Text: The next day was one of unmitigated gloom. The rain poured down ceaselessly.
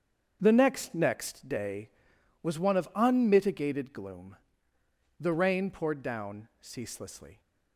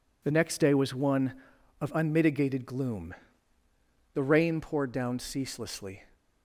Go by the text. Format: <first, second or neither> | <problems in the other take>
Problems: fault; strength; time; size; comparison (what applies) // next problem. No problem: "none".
second | starts louder than the rest; strong; until 1.4 s; 7 dB // says "next" twice; at 0.9 s